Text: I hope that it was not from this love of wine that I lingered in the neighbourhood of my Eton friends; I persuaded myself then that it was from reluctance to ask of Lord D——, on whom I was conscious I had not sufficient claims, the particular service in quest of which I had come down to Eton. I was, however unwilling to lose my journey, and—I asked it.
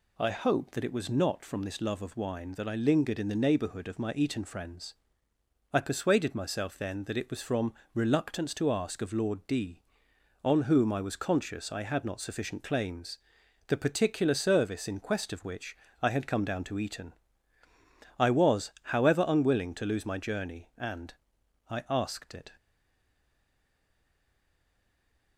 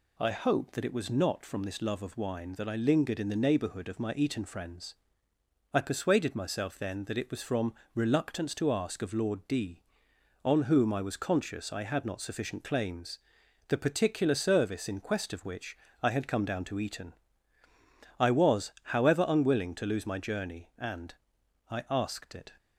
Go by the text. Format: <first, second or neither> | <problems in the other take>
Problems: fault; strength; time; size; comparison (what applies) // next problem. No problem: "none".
second | pauses between "from" and "reluctance"; slight; at 7.7 s; 0.18 s long; slight in the second // pauses between "which" and "I"; slight; at 15.7 s; 0.24 s long; slight in the second // stays silent after the last word; strong; from 22.5 s on; 2.8 s long